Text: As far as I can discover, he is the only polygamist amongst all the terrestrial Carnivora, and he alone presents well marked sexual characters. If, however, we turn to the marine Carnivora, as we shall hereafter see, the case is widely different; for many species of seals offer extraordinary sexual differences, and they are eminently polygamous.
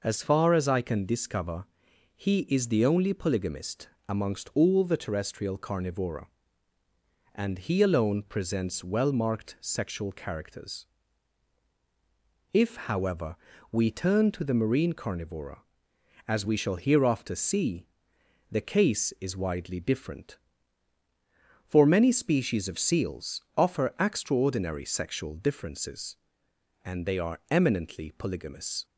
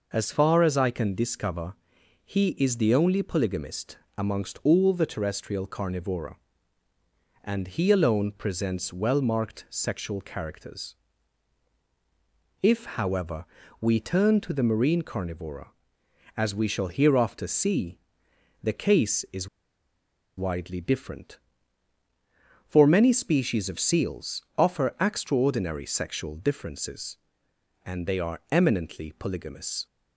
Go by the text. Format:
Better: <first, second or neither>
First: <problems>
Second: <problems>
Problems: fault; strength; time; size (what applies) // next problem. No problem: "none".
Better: first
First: pauses between "polygamist" and "amongst"; slight; at 3.8 s; 0.20 s long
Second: pauses between "polygamist" and "amongst"; slight; at 3.9 s; 0.20 s long // pauses between "is" and "widely"; noticeable; at 19.4 s; 0.89 s long